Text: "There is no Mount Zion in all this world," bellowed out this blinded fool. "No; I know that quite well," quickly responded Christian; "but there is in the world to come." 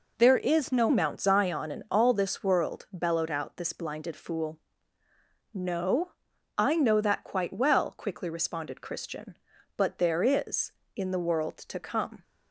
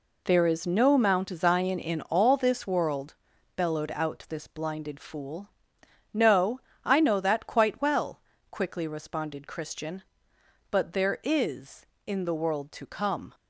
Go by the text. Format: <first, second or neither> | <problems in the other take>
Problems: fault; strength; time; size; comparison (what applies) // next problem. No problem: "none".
second | changes voice at "Mount"; from 0.8 s on; 11.4 s long